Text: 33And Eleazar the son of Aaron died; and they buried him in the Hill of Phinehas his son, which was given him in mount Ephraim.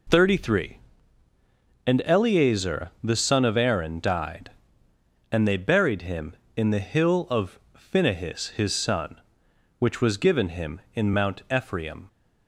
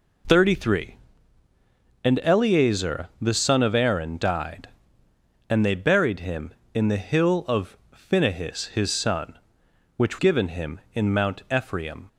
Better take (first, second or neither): first